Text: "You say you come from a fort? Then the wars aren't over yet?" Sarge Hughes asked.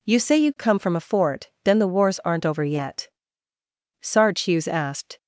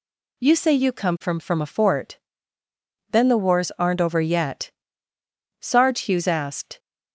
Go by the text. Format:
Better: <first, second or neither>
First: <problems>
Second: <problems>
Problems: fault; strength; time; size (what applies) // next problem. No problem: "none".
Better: first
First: none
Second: says "from" twice; at 1.4 s